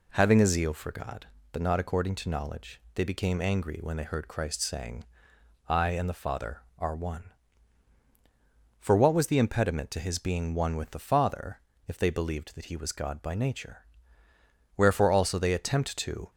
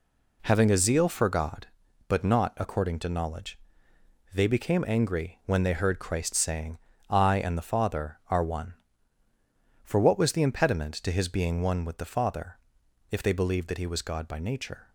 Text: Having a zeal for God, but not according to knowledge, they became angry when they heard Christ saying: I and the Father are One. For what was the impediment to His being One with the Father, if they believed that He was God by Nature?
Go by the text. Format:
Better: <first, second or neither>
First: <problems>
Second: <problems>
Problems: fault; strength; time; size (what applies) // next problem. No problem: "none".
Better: second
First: goes on to say "Wherefore also they attempt to"; from 14.7 s on; 1.5 s long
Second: none